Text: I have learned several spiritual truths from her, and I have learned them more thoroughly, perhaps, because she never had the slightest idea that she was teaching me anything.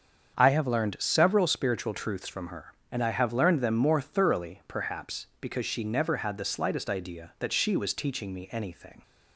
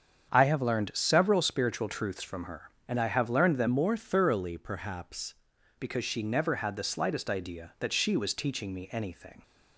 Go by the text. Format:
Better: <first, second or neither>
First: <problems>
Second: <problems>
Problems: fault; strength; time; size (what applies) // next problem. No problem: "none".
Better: first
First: starts louder than the rest; strong; until 1.3 s; 7 dB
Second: starts louder than the rest; strong; until 1.3 s; 7.5 dB // changes voice from "more" to "perhaps"; from 3.6 to 5.3 s; 1.7 s long